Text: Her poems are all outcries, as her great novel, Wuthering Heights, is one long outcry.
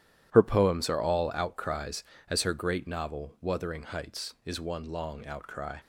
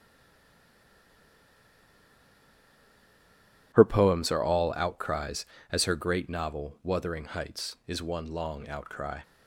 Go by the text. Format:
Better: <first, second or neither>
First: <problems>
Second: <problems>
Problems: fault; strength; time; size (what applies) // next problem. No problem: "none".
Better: first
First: starts louder than the rest; strong; until 1.3 s; 11.5 dB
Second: stays silent before the first word; strong; until 3.7 s; 3.7 s long // starts louder than the rest; strong; until 4.7 s; 11.5 dB